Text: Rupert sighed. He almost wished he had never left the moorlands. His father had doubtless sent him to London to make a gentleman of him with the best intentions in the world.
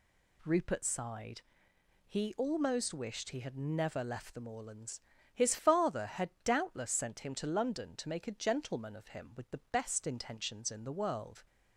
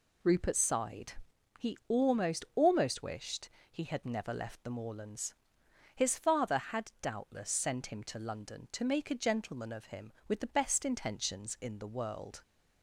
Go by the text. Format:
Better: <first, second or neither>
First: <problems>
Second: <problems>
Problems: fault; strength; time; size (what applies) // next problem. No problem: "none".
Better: first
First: none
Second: says "almost" twice; at 2.5 s // pauses between "wished" and "he"; slight; at 3.4 s; 0.22 s long